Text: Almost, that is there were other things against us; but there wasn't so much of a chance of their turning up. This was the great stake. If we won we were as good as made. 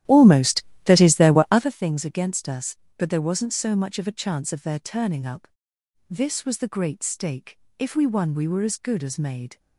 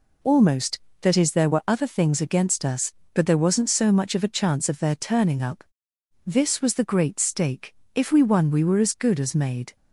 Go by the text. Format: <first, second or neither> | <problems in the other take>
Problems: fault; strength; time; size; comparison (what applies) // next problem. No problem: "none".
second | starts louder than the rest; strong; until 1.8 s; 12.5 dB